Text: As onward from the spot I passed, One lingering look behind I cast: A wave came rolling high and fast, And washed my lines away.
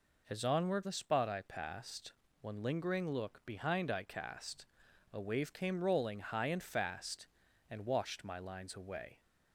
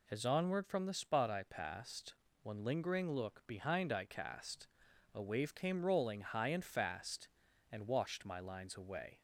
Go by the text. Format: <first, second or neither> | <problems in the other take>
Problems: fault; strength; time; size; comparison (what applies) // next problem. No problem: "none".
second | skips "from"; at 0.8 s